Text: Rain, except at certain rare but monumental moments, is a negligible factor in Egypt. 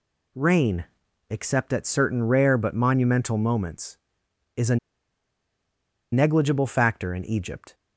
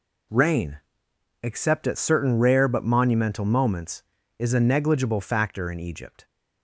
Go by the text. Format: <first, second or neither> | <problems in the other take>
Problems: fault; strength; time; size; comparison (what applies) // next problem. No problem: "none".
second | pauses between "a" and "negligible"; strong; at 4.7 s; 1.3 s long